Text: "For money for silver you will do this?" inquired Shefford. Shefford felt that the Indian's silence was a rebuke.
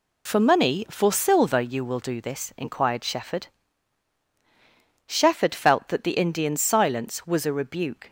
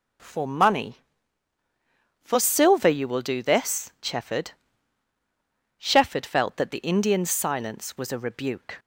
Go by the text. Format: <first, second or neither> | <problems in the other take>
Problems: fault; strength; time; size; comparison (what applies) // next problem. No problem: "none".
first | skips "inquired"; at 3.9 s